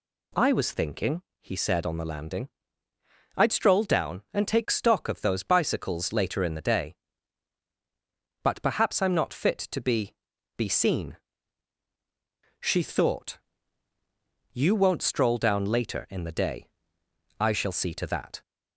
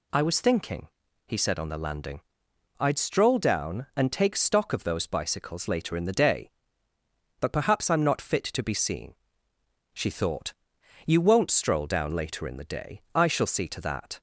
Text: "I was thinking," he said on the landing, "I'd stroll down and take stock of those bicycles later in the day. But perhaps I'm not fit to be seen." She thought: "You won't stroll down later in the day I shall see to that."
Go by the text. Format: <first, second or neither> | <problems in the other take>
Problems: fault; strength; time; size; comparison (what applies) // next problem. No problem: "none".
second | says "be" twice; at 10.5 s // pauses between "day" and "I"; noticeable; at 16.6 s; 0.72 s long